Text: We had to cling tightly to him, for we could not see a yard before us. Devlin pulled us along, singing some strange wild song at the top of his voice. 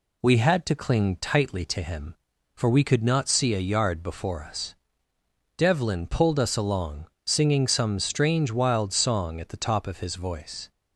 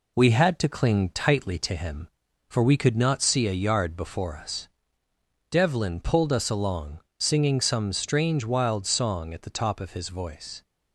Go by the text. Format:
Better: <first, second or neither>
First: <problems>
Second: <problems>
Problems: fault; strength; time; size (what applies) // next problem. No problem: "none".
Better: first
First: none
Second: gets quieter; throughout; 3.5 dB